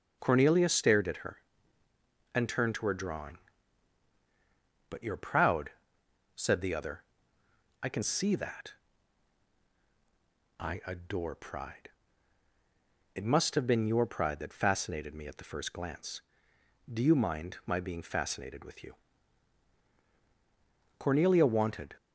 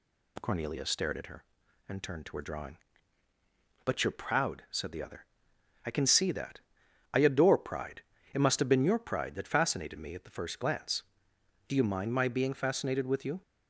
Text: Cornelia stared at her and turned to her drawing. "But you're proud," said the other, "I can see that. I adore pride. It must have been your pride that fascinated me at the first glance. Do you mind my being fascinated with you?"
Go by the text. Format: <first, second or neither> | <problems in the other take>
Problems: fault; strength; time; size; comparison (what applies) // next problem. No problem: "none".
second | starts louder than the rest; noticeable; until 1.2 s; 6 dB // goes on to say "Cornelia wanted"; noticeable; from 20.9 s on; 0.98 s long